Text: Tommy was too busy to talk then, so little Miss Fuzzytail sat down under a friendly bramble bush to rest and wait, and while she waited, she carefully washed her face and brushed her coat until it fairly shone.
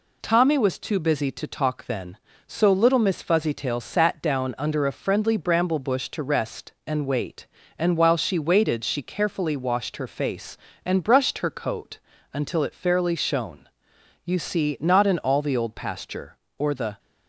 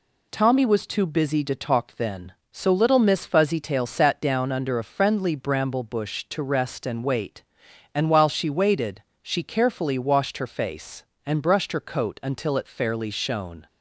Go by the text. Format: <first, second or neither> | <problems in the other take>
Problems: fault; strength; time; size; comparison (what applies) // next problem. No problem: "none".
second | pauses between "coat" and "until"; slight; at 11.9 s; 0.34 s long // goes on to say "You see not in all the Old Pasture or the"; strong; from 14.2 s on; 2.7 s long